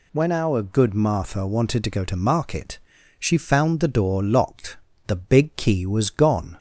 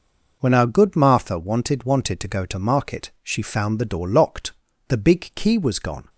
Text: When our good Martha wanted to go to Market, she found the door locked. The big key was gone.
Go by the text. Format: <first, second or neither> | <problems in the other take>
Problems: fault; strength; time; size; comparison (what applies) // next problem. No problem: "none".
first | says "wanted" twice; at 1.8 s